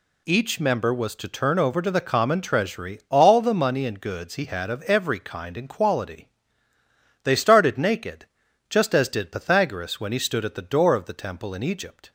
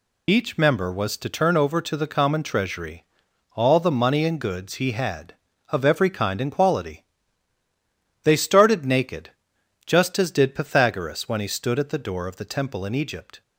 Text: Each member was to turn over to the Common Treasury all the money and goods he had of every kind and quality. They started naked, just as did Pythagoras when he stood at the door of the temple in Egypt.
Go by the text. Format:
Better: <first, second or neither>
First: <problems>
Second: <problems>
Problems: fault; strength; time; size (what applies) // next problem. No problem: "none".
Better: first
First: none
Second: loses the start of "Each"; at 0.2 s; 45 ms // pauses between "Treasury" and "all"; noticeable; at 3.0 s; 0.50 s long